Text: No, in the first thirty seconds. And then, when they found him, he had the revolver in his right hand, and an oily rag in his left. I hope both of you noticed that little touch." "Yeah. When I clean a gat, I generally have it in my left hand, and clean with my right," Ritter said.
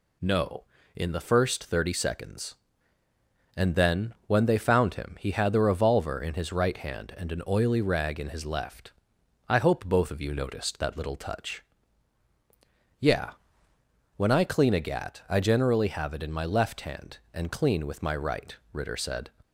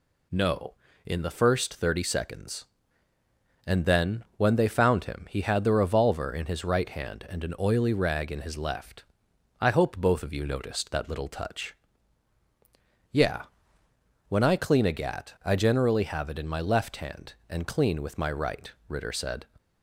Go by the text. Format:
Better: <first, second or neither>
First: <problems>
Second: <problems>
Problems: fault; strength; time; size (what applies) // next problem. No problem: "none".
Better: neither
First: none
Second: none